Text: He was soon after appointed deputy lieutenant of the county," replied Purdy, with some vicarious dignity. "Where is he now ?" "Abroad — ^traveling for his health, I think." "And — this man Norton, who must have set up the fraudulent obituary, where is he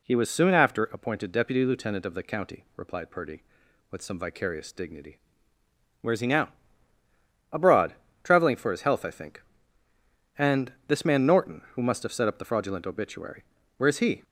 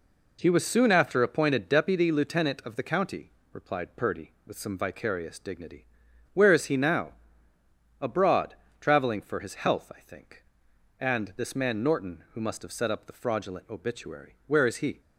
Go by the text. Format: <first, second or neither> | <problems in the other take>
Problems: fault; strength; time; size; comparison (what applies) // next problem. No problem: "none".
neither | none